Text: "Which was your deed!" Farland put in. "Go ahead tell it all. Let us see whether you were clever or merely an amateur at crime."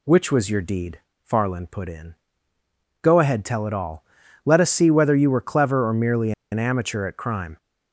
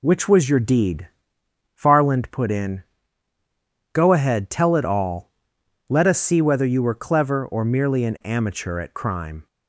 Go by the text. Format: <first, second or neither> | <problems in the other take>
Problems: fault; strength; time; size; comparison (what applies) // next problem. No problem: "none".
second | pauses between "merely" and "an"; slight; at 6.3 s; 0.20 s long